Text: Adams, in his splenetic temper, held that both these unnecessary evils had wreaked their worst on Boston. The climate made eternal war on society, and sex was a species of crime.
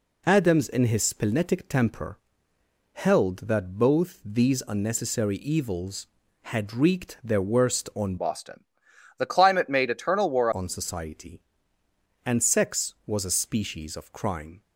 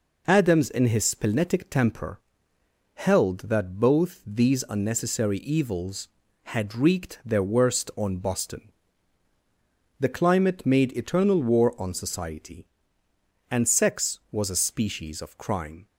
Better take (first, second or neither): second